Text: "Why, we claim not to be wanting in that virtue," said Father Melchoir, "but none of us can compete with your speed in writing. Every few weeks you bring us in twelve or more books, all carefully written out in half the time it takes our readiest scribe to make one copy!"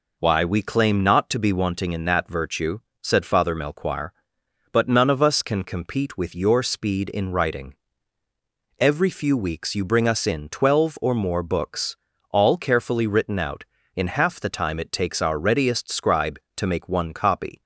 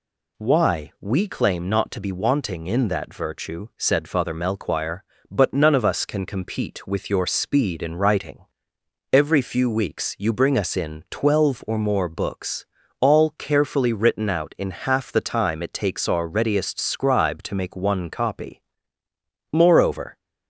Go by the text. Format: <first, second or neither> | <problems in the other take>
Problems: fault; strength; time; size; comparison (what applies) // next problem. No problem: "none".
first | goes on to say "Moreover"; noticeable; from 19.5 s on; 0.64 s long